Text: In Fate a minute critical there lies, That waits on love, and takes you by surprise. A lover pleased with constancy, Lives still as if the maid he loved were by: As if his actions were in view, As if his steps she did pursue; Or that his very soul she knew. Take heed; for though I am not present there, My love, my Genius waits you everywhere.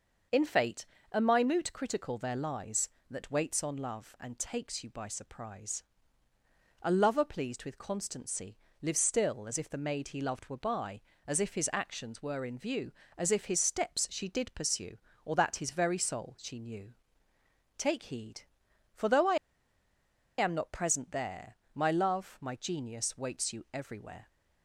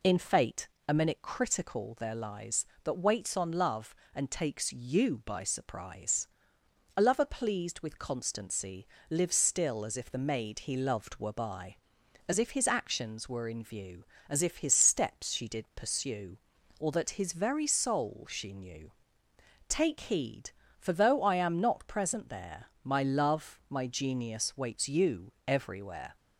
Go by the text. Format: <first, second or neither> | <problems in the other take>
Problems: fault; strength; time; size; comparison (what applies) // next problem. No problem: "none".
second | starts louder than the rest; noticeable; until 1.5 s; 6 dB // pauses between "Fate" and "a"; slight; at 0.8 s; 0.26 s long; slight in the second // pauses between "I" and "am"; at 19.3 s; 1.0 s long